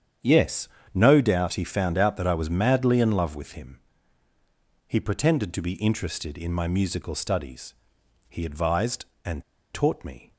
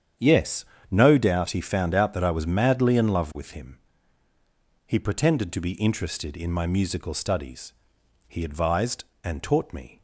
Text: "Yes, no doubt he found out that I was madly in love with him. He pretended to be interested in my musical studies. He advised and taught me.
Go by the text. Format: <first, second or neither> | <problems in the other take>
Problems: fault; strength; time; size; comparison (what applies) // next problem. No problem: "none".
second | starts louder than the rest; strong; until 1.4 s; 8.5 dB; strong in the second // pauses between "and" and "taught"; slight; at 9.4 s; 0.30 s long